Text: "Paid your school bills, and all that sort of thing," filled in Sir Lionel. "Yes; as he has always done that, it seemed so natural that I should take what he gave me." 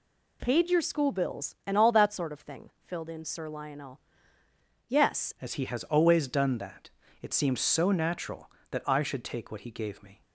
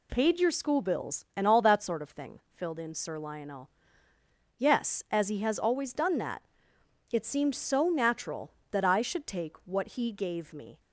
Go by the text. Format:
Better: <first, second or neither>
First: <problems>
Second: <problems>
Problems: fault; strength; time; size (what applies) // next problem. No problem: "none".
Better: second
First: changes voice at "as"; from 5.4 s on; 4.8 s long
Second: none